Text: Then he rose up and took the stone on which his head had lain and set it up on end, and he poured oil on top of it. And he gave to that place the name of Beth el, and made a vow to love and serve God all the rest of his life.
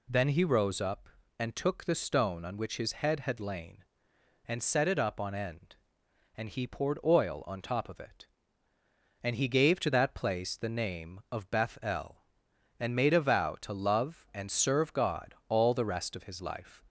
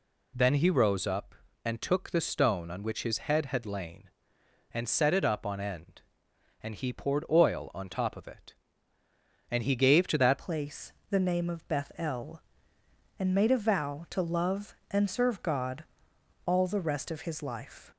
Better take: first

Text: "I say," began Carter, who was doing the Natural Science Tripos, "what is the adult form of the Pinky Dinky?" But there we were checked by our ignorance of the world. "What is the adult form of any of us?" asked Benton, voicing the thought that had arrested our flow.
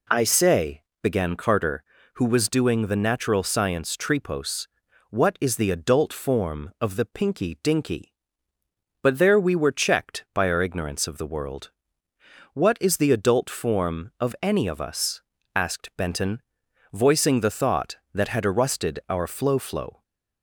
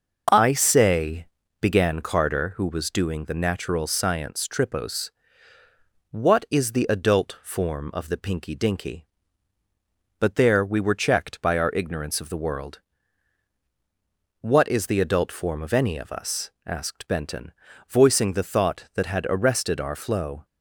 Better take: second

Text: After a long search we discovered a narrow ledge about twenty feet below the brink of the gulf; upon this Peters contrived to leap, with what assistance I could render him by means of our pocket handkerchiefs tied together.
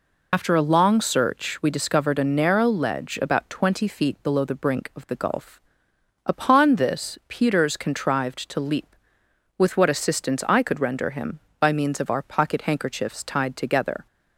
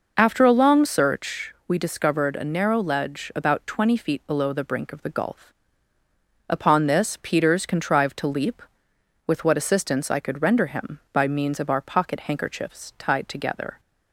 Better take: second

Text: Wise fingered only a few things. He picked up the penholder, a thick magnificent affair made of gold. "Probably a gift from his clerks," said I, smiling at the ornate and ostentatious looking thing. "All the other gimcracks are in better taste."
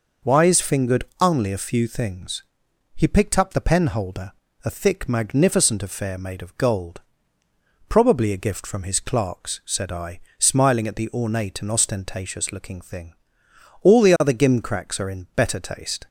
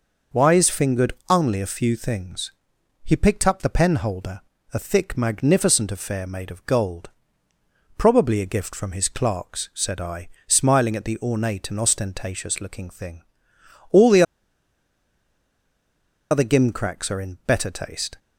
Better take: first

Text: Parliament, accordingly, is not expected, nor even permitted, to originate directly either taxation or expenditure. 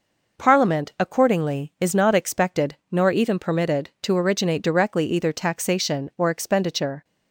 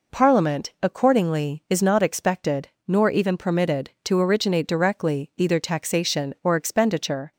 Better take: neither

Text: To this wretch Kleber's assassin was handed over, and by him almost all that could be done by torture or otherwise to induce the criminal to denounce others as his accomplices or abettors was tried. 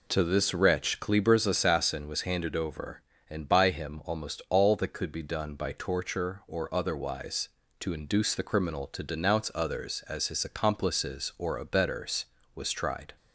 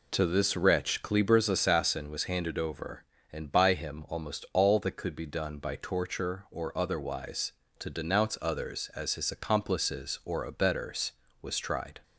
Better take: first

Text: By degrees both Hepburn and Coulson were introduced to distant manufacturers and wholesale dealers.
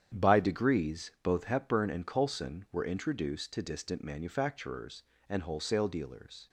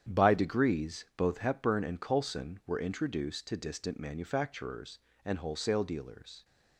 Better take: neither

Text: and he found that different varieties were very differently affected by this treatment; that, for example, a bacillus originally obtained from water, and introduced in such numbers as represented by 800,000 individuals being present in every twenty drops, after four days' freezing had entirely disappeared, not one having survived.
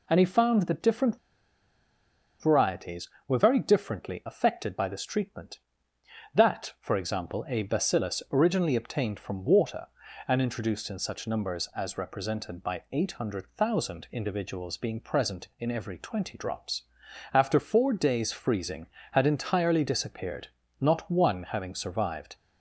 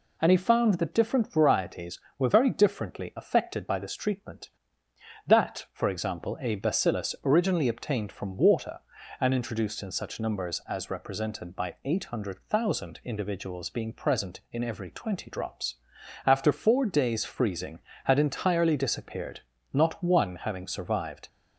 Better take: second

